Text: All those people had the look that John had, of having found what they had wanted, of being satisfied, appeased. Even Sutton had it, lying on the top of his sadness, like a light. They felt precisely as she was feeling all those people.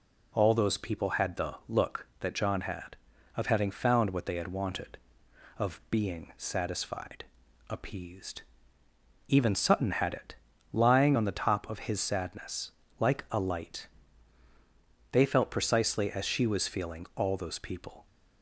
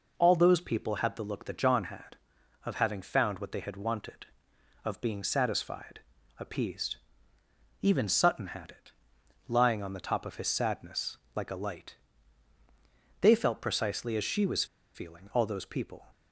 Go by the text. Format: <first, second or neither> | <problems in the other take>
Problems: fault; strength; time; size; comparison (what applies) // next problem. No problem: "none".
first | pauses between "was" and "feeling"; slight; at 14.6 s; 0.29 s long